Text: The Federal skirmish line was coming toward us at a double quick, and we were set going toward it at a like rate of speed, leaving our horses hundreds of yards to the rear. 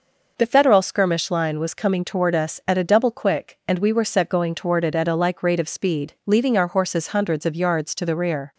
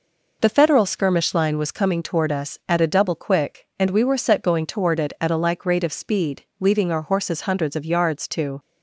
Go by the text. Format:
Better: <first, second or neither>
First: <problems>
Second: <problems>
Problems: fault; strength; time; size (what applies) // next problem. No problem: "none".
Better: first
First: none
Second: stops before "the rear"; at 8.5 s